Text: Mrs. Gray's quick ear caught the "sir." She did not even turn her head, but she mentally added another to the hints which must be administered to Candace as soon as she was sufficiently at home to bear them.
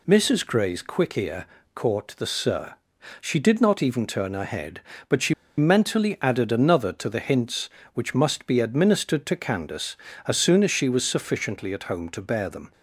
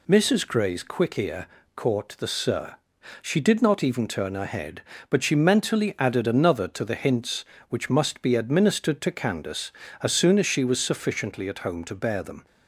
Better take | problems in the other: second | pauses between "ear" and "caught"; slight; at 1.4 s; 0.28 s long; slight in the second // pauses between "she" and "mentally"; slight; at 5.3 s; 0.23 s long

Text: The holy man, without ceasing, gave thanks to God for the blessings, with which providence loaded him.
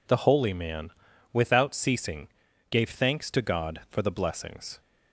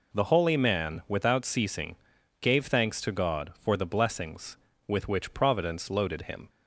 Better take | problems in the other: second | stops before "with which providence loaded him"; at 4.7 s

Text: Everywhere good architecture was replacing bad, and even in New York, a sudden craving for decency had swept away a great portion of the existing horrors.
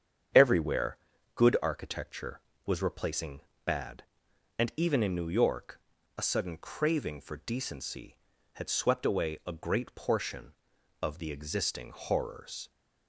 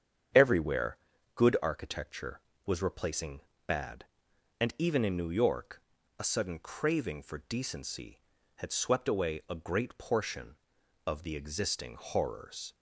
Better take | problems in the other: neither | starts louder than the rest; strong; the same in both // pauses between "Everywhere" and "good"; the same in both // pauses between "replacing" and "bad"; slight; the same in both

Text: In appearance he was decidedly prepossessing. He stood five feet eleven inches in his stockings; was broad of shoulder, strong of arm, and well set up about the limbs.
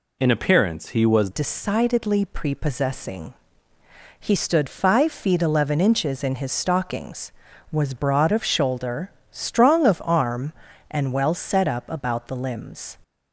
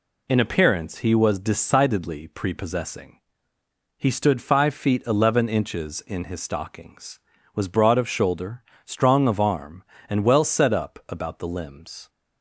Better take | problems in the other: second | changes voice at "decidedly"; from 1.3 s on; 11.6 s long

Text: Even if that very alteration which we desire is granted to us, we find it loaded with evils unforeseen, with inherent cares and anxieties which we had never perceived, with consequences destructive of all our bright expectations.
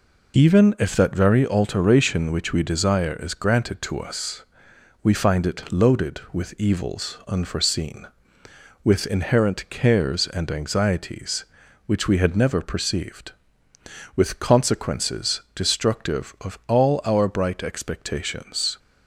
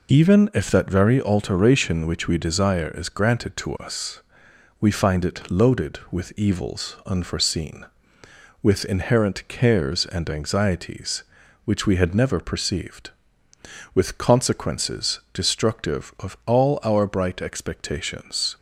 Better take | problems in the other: neither | none

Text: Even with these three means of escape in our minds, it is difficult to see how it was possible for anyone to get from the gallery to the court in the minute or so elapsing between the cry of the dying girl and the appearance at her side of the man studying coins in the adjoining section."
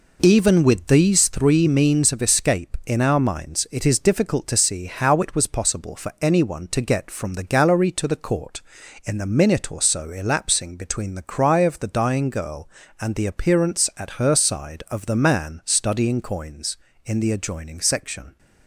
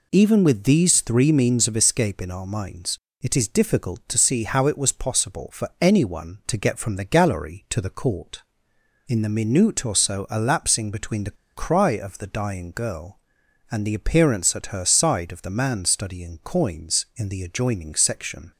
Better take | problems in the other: first | pauses between "the" and "cry"; slight; at 11.3 s; 0.22 s long

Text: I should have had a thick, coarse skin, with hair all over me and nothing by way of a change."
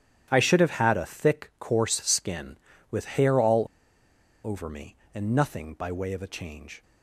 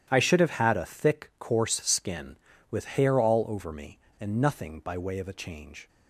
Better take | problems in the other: second | starts louder than the rest; strong; until 1.3 s; 11 dB; strong in the second // pauses between "all" and "over"; noticeable; at 3.6 s; 0.79 s long

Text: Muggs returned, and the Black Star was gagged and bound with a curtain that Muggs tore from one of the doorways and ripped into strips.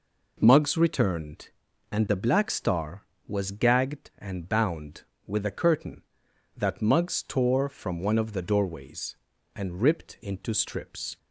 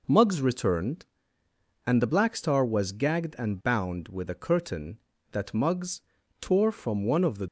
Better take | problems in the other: first | pauses between "Muggs" and "tore"; at 6.0 s; 0.40 s long // stops before "doorways and ripped into strips"; at 7.4 s

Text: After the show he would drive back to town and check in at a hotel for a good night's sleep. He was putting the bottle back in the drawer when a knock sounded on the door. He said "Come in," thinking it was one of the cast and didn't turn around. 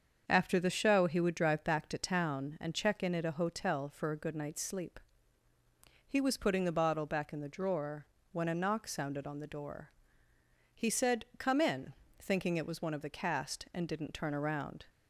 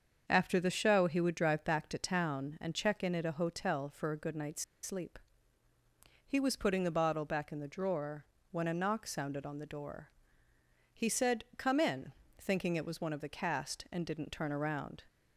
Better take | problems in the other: first | starts louder than the rest; until 1.2 s; 7 dB; also in the first // pauses between "night's" and "sleep"; slight; at 4.6 s; 0.20 s long // pauses between "drawer" and "when"; slight; at 8.2 s; 0.26 s long; slight in the first

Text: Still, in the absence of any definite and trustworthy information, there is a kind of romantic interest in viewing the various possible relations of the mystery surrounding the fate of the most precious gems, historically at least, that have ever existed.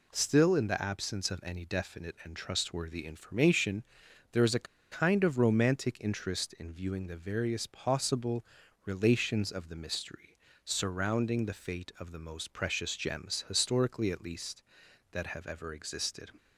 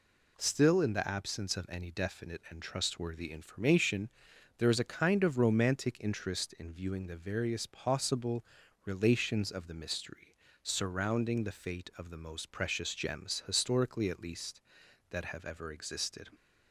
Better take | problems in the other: second | pauses between "a" and "kind"; slight; at 4.6 s; 0.26 s long // pauses between "possible" and "relations"; at 8.4 s; 0.42 s long; also in the second // pauses between "mystery" and "surrounding"; slight; at 10.2 s; 0.36 s long; slight in the second

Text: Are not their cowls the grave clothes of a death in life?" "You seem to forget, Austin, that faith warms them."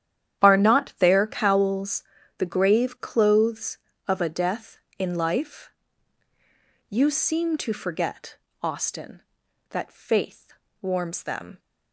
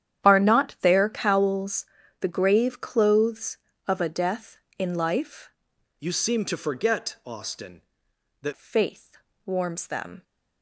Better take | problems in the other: first | starts louder than the rest; strong; until 1.3 s; 10 dB; strong in the first // pauses between "cowls" and "the"; slight; at 1.8 s; 0.34 s long; slight in the first // changes voice from "You" to "that"; from 5.9 to 8.5 s; 2.6 s long // pauses between "faith" and "warms"; slight; at 9.1 s; 0.28 s long; slight in the first

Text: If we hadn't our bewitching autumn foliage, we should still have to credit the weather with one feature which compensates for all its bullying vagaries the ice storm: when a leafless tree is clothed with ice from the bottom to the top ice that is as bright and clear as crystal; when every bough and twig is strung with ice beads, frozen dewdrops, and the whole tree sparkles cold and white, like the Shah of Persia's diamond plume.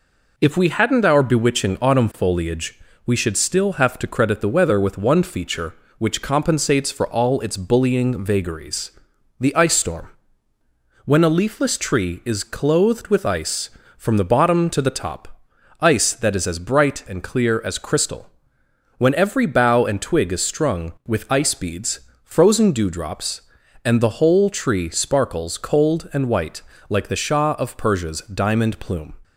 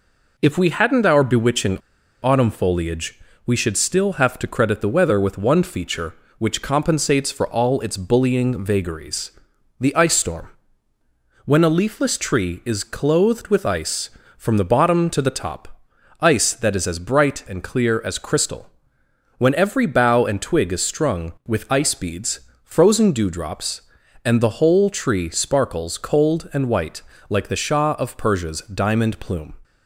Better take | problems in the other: first | pauses between "bewitching" and "autumn"; at 1.7 s; 0.43 s long // pauses between "vagaries" and "the"; noticeable; at 9.3 s; 0.48 s long; noticeable in the first // pauses between "top" and "ice"; at 15.8 s; 0.38 s long; also in the first

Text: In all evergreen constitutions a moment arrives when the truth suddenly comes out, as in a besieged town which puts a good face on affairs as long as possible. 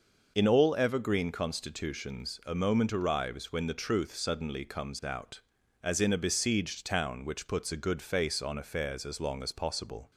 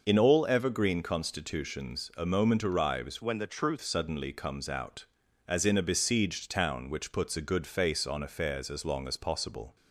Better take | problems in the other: first | changes voice from "when" to "truth"; from 3.2 to 3.7 s; 0.5 s long

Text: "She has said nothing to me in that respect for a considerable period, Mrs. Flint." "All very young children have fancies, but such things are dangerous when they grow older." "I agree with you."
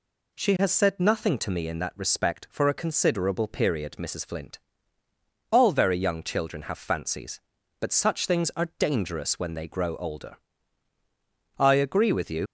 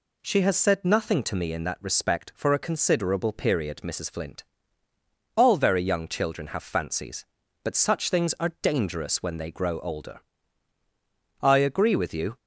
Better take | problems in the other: second | leaves "you" unfinished; at 12.4 s; 70 ms

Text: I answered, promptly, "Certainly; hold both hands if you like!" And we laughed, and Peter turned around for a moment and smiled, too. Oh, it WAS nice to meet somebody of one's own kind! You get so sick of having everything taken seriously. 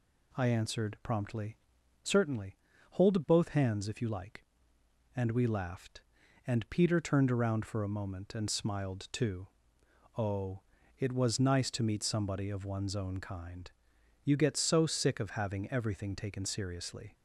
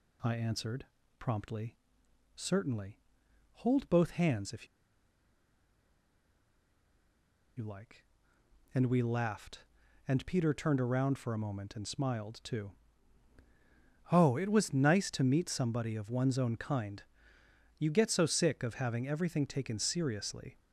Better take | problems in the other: first | pauses between "if" and "you"; strong; at 4.6 s; 2.9 s long

